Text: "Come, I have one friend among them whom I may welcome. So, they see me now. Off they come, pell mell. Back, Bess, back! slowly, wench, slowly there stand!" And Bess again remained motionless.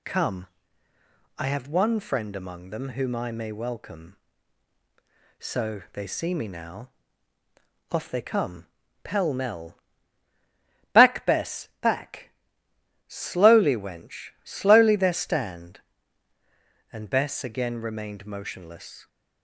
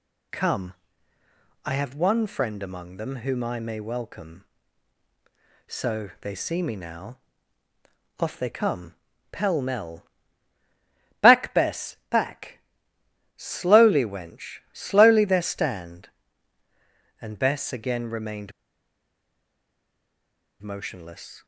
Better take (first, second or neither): first